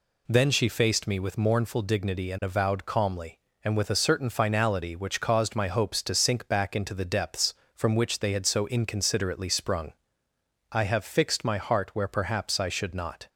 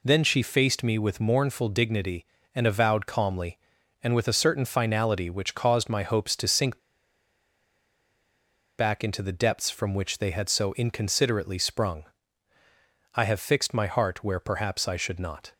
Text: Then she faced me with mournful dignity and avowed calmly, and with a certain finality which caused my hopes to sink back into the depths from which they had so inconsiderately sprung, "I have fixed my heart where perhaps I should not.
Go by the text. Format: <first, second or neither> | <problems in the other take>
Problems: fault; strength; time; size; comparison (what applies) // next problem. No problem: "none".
first | pauses between "sink" and "back"; strong; at 6.7 s; 2.0 s long